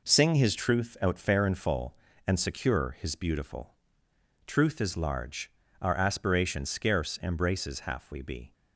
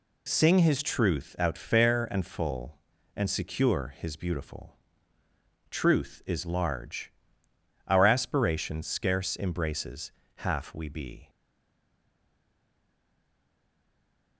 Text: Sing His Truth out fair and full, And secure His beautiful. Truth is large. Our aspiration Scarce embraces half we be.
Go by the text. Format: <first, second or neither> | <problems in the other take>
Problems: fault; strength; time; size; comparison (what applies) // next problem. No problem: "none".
first | pauses between "embraces" and "half"; slight; at 10.1 s; 0.24 s long // stays silent after the last word; strong; from 11.2 s on; 3.1 s long